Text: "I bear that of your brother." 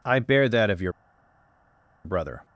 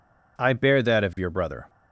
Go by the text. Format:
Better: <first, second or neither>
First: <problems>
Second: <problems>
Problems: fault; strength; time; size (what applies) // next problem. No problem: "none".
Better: second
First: pauses between "your" and "brother"; at 0.9 s; 1.1 s long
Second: none